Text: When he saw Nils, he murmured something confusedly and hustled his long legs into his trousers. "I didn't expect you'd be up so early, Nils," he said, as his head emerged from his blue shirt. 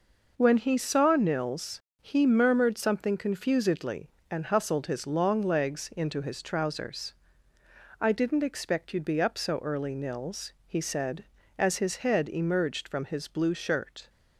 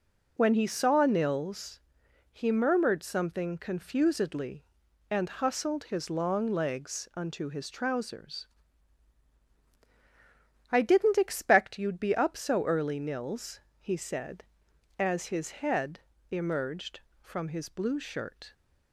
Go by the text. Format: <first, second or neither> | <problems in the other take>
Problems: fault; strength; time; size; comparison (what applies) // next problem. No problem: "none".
first | says "unto" for "into"; at 7.1 s // pauses between "head" and "emerged"; slight; at 16.0 s; 0.28 s long